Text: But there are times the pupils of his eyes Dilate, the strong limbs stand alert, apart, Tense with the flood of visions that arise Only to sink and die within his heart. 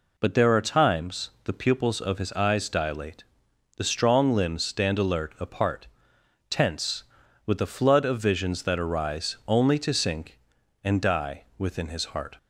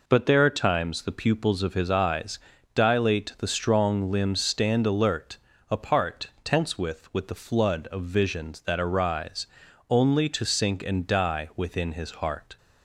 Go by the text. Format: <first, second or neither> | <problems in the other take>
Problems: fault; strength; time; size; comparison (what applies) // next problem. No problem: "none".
first | pauses between "eyes" and "Dilate"; at 2.3 s; 0.38 s long // says "with" twice; at 7.1 s // pauses between "arise" and "Only"; at 9.4 s; 0.42 s long